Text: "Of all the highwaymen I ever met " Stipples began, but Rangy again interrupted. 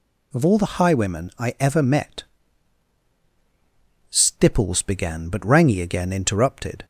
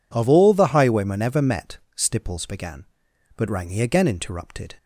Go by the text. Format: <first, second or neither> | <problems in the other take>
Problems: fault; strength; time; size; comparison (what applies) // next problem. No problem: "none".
first | skips "I"; at 1.2 s